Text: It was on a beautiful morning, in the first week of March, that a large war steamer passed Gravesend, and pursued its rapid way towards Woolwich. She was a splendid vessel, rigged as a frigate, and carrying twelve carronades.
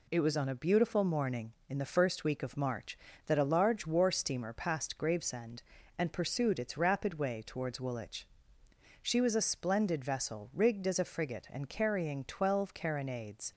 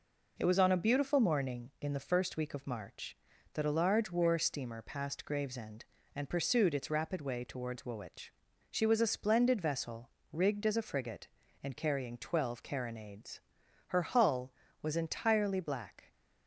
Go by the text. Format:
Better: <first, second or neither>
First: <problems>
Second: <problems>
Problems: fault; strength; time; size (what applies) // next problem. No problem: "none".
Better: first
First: none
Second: goes on to say "Her hull was entirely black"; strong; from 13.8 s on; 2.2 s long